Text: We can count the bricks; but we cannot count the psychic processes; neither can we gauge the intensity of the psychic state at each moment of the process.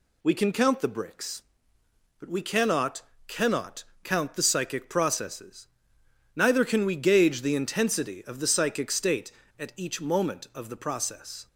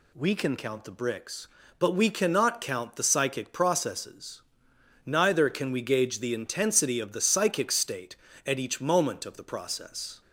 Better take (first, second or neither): second